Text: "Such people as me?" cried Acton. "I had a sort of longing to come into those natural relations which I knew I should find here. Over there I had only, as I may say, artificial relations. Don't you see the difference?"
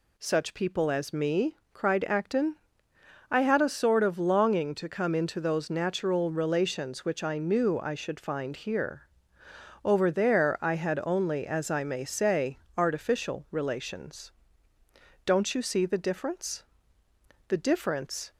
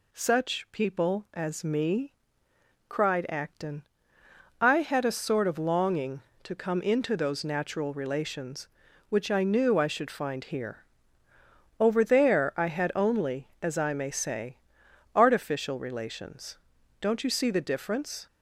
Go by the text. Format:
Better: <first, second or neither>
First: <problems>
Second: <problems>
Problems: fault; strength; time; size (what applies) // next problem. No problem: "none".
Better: second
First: goes on to say "The difference"; noticeable; from 17.4 s on; 0.84 s long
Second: none